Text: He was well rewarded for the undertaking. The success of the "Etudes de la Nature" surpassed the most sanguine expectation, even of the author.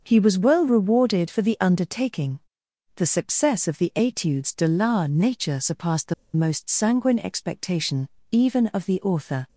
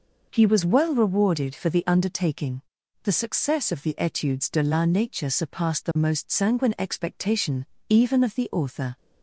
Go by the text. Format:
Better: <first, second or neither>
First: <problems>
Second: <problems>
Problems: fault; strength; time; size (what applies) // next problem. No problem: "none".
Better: second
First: starts louder than the rest; noticeable; until 1.0 s; 6 dB // pauses between "the" and "most"; slight; at 6.1 s; 0.22 s long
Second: none